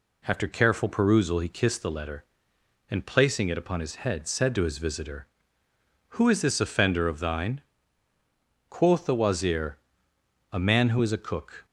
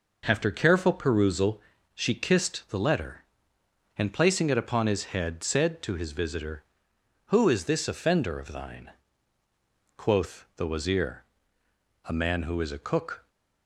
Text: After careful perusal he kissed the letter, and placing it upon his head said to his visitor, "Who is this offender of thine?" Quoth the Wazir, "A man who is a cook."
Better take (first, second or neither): first